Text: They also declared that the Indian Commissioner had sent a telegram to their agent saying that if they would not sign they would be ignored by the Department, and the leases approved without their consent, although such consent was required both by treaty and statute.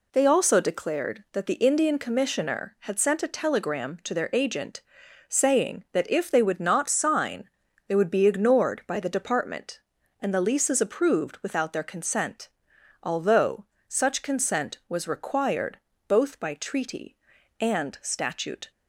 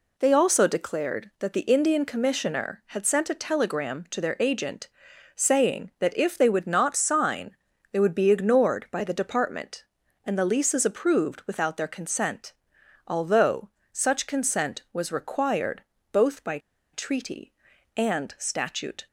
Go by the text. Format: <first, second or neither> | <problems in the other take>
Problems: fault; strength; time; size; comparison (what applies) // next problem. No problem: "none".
first | pauses between "agent" and "saying"; noticeable; at 4.8 s; 0.46 s long; noticeable in the first // pauses between "sign" and "they"; at 7.5 s; 0.38 s long; also in the first // pauses between "although" and "such"; slight; at 13.6 s; 0.24 s long; slight in the first // pauses between "required" and "both"; slight; at 15.8 s; 0.30 s long; slight in the first // pauses between "by" and "treaty"; slight; at 16.5 s; 0.34 s long